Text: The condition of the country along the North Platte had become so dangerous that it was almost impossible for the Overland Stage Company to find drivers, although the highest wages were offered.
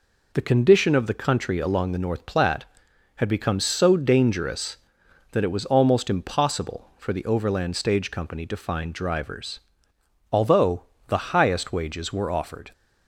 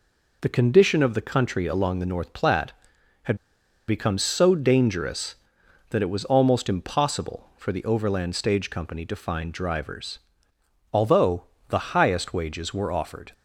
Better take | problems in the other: first | pauses between "had" and "become"; noticeable; at 3.3 s; 0.52 s long // pauses between "although" and "the"; slight; at 11.4 s; 0.24 s long; slight in the first

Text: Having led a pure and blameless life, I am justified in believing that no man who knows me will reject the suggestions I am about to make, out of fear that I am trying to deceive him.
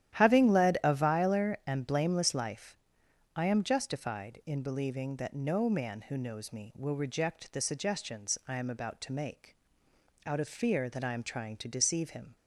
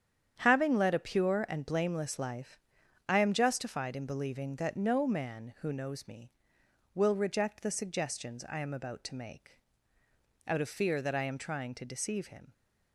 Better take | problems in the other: second | starts louder than the rest; strong; until 1.2 s; 11.5 dB; strong in the second // says "viler" for "pure"; at 0.9 s

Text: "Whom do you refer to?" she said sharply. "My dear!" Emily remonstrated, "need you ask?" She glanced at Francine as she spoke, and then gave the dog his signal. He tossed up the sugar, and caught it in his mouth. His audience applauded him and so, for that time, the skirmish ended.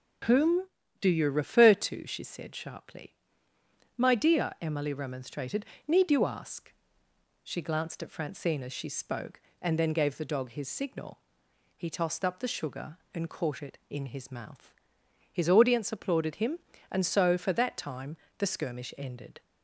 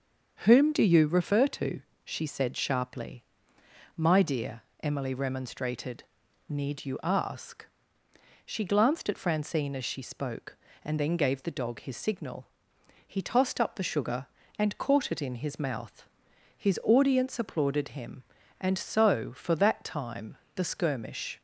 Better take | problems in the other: first | starts louder than the rest; until 1.3 s; 6.5 dB // stops before "ended"; at 21.3 s

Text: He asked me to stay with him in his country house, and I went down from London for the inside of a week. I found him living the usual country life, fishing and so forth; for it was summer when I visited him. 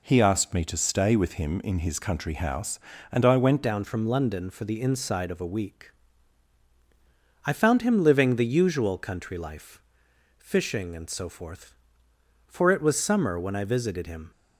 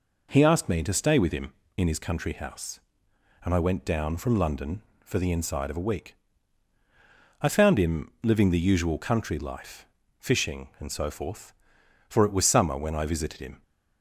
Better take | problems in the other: second | changes voice at "down"; from 3.6 s on; 10.7 s long

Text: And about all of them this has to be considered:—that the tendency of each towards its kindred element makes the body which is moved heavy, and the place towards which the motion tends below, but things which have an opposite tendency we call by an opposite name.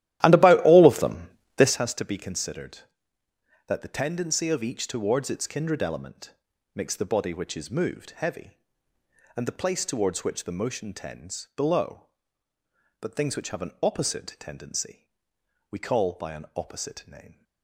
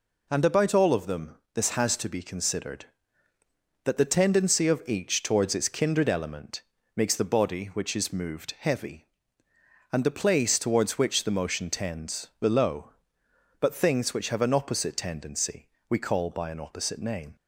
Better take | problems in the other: second | starts louder than the rest; strong; until 1.8 s; 13.5 dB // pauses between "them" and "this"; slight; at 1.2 s; 0.28 s long; slight in the second // pauses between "element" and "makes"; at 6.3 s; 0.40 s long; slight in the second // pauses between "tendency" and "we"; noticeable; at 15.0 s; 0.62 s long; slight in the second

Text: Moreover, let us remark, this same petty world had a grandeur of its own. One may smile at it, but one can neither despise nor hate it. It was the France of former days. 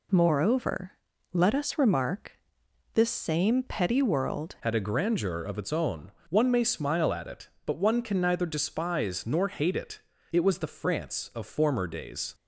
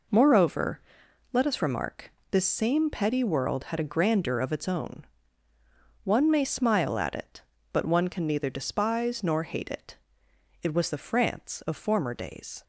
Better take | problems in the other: second | changes voice at "had"; from 4.6 s on; 7.7 s long

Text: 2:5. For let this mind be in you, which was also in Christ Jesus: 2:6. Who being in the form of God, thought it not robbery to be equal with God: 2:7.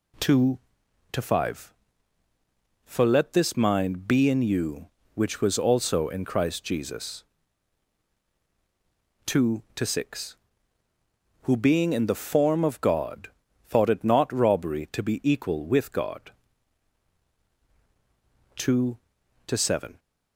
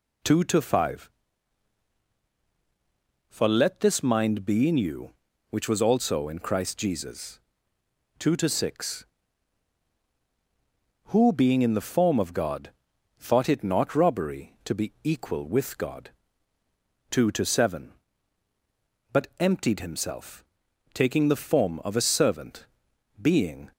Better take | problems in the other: first | goes on to say "But emptied himself taking the form of a servant being"; strong; from 19.1 s on; 4.6 s long

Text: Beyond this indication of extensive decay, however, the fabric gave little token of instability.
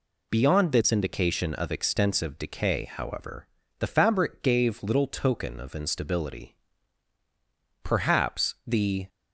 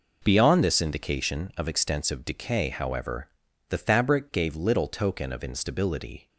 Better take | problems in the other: second | goes on to say "Perhaps the"; noticeable; from 7.8 s on; 1.2 s long

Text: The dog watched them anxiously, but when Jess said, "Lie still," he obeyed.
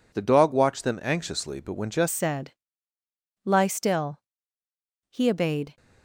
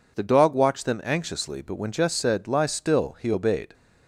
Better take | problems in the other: second | changes voice at "said"; from 2.1 s on; 3.6 s long

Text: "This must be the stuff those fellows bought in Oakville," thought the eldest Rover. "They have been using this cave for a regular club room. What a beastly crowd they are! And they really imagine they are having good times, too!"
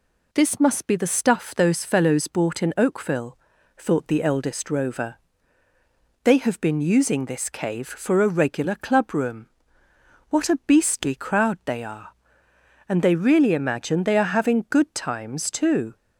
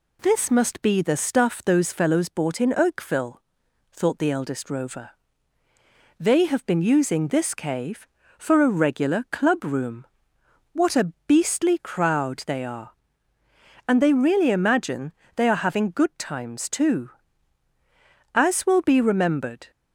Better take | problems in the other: first | pauses between "imagine" and "they"; slight; at 15.1 s; 0.24 s long // goes on to say "As will be remembered"; from 18.3 s on; 1.3 s long

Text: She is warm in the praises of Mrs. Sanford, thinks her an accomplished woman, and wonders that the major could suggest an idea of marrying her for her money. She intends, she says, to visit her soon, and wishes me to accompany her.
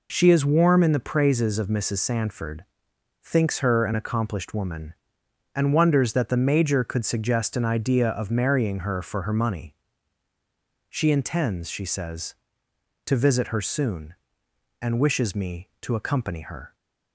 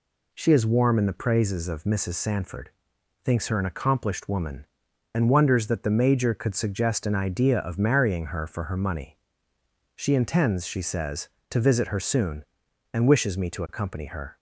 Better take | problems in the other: neither | none

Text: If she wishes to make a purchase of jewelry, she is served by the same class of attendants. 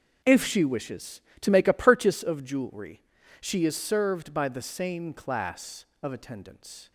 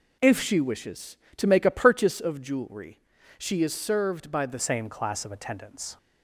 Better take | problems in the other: first | changes voice at "same"; from 4.5 s on; 1.4 s long

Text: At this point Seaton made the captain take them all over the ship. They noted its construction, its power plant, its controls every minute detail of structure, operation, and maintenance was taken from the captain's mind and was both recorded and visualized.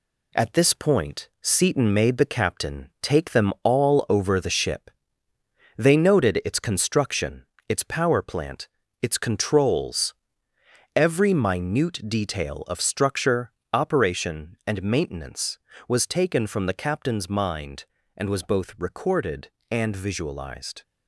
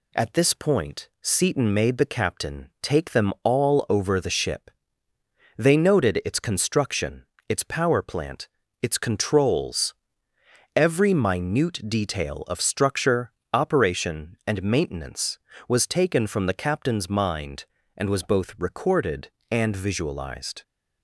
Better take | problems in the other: second | gets quieter; noticeable; throughout; 4.5 dB // pauses between "controls" and "every"; noticeable; at 10.1 s; 0.82 s long; noticeable in the second

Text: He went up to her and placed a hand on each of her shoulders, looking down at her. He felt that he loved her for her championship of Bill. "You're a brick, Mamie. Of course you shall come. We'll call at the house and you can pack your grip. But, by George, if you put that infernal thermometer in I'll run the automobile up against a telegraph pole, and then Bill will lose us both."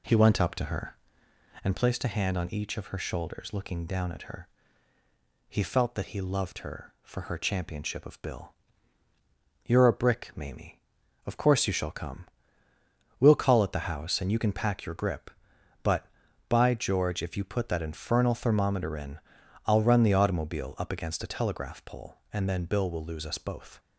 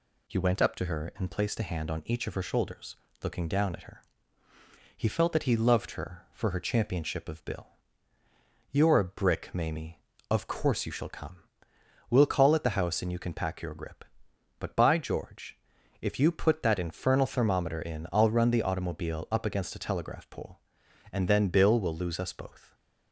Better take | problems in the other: second | starts louder than the rest; slight; until 1.8 s; 2.5 dB // pauses between "in" and "I'll"; noticeable; at 19.1 s; 0.48 s long

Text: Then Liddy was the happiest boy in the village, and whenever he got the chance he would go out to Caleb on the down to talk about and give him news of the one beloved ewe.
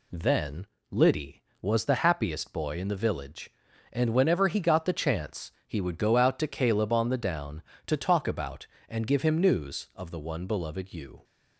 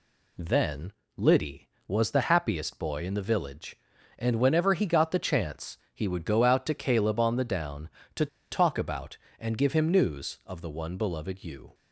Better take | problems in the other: first | pauses between "Then" and "Liddy"; slight; at 0.9 s; 0.24 s long; slight in the first // pauses between "chance" and "he"; slight; at 5.7 s; 0.16 s long; slight in the first // pauses between "to" and "talk"; slight; at 8.2 s; 0.24 s long

